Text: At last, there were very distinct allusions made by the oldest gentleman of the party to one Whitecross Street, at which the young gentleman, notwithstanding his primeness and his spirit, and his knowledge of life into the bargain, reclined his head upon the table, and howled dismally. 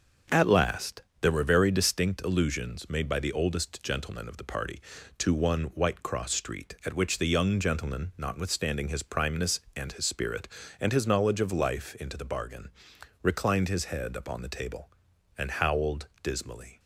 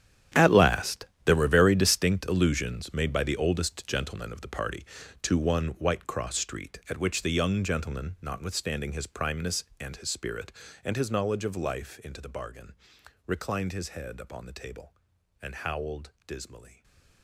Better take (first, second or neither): first